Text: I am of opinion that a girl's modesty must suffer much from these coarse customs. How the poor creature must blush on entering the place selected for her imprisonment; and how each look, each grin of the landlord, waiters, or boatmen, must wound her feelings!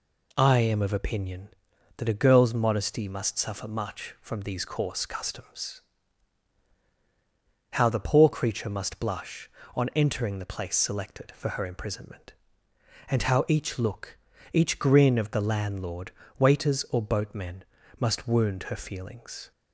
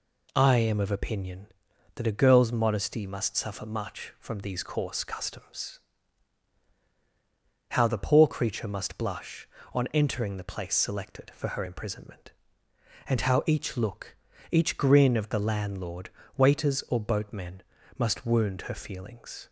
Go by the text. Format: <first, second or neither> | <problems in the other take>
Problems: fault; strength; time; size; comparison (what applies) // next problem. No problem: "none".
neither | none